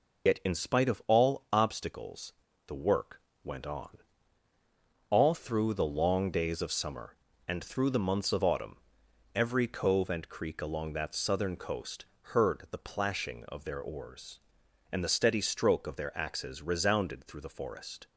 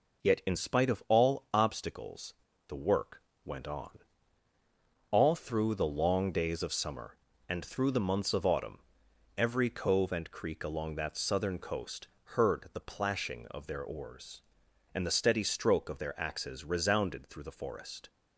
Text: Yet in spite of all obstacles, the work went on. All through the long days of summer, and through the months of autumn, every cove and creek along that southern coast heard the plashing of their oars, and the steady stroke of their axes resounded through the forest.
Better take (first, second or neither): second